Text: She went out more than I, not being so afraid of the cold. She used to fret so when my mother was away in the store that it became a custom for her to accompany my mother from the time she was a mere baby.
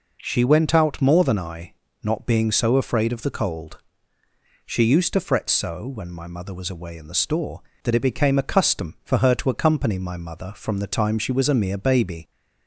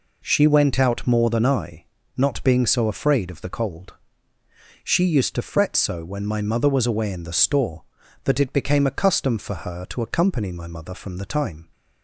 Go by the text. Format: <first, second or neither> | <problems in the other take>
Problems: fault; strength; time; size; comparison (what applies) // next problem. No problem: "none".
first | stops before "she was a mere baby"; at 11.7 s